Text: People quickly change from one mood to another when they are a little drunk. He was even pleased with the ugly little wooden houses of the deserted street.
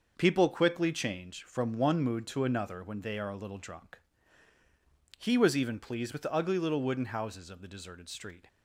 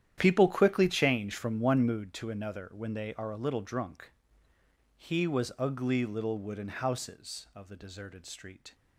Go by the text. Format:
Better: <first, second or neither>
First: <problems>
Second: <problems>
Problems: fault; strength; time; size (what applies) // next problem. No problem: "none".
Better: first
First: starts louder than the rest; noticeable; until 1.1 s; 6 dB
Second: starts louder than the rest; strong; until 1.1 s; 10.5 dB // skips "even pleased with the"; at 5.5 s